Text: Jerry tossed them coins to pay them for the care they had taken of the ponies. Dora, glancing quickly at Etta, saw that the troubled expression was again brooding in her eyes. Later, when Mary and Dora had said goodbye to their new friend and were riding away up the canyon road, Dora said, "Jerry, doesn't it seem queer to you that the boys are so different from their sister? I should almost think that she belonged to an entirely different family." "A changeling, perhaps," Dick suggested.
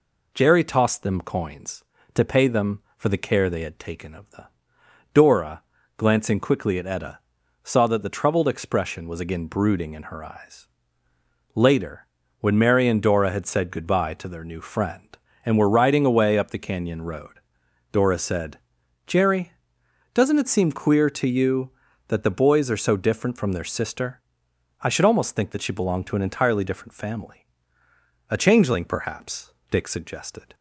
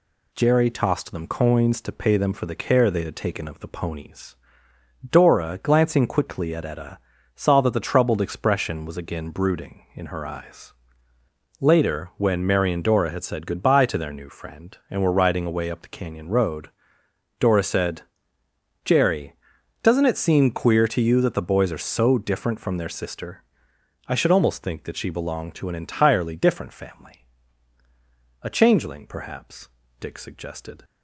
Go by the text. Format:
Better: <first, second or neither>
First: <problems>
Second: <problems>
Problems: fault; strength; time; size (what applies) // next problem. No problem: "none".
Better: second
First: skips "ponies"; at 4.8 s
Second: none